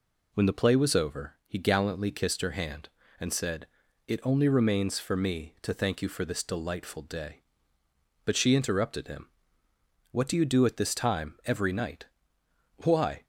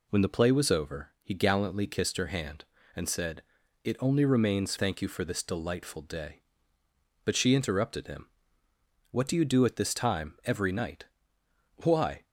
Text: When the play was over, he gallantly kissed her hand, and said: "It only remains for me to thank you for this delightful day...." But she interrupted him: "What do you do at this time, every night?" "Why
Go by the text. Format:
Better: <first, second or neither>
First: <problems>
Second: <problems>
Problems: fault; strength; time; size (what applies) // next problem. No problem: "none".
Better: first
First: none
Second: skips "for me to"; at 4.7 s